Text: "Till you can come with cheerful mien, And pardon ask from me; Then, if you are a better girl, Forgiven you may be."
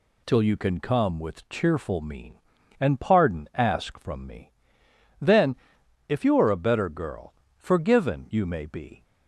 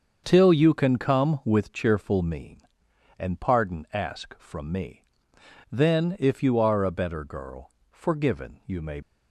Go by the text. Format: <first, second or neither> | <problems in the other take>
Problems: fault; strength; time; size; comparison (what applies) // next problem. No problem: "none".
first | starts louder than the rest; until 1.2 s; 6.5 dB // stops before "be"; at 9.0 s